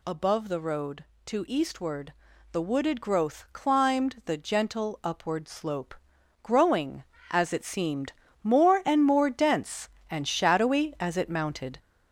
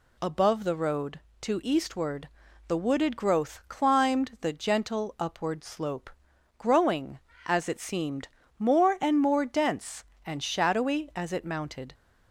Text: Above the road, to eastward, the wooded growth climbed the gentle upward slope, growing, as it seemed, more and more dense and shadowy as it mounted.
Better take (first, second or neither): second